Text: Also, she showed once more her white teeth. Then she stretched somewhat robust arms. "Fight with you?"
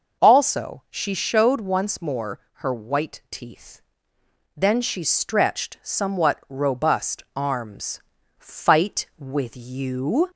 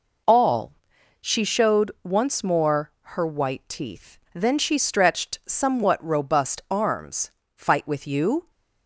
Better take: first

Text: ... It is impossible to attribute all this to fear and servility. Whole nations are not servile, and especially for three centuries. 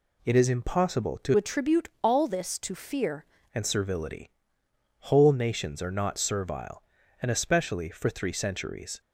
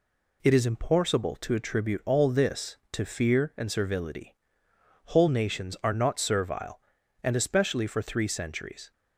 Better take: second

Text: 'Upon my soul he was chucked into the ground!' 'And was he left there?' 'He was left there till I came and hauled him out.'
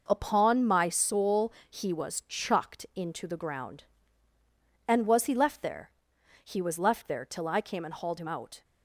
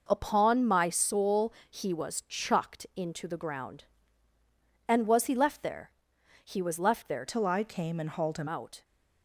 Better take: first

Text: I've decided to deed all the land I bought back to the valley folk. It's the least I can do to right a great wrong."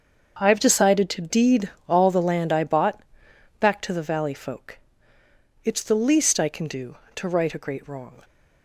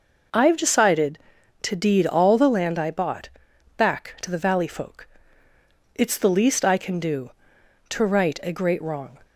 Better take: second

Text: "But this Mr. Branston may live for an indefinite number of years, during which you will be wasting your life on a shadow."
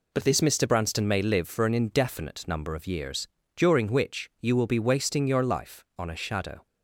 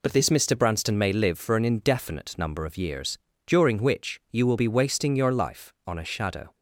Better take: neither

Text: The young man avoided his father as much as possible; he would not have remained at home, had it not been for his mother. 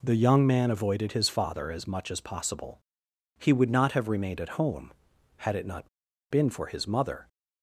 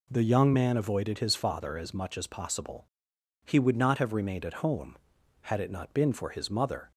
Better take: second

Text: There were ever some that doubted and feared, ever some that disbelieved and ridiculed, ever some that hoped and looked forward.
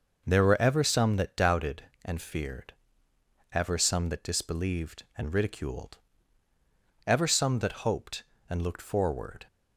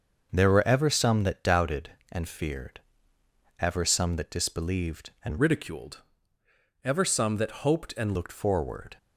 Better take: first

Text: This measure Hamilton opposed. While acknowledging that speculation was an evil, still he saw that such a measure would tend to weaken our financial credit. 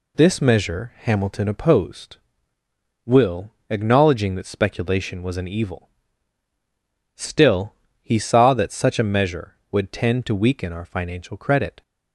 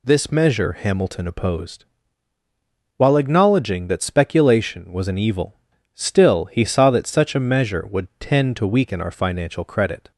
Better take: second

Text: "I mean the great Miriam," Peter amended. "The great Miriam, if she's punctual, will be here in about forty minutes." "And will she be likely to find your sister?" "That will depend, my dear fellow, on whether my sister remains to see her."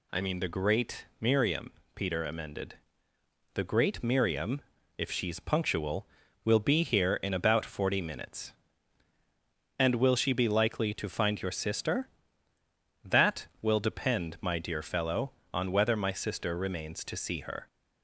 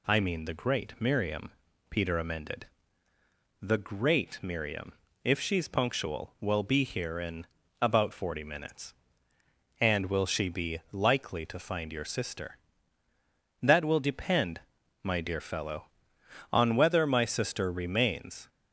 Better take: first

